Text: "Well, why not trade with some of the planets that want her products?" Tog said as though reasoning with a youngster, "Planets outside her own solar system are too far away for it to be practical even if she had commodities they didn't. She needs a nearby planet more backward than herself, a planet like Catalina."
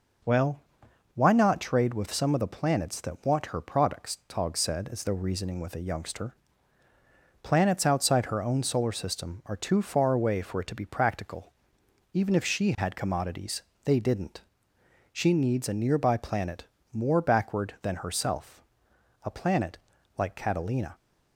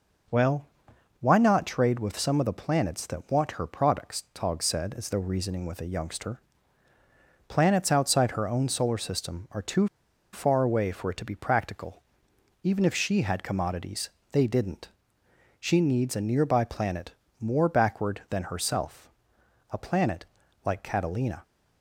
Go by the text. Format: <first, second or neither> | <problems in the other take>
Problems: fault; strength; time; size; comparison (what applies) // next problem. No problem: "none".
first | pauses between "too" and "far"; at 9.8 s; 0.44 s long // pauses between "practical" and "even"; noticeable; at 12.0 s; 0.62 s long; noticeable in the first // pauses between "commodities" and "they"; slight; at 14.0 s; 0.22 s long; slight in the first // pauses between "planet" and "more"; slight; at 17.1 s; 0.26 s long; slight in the first // pauses between "planet" and "like"; at 20.2 s; 0.40 s long; also in the first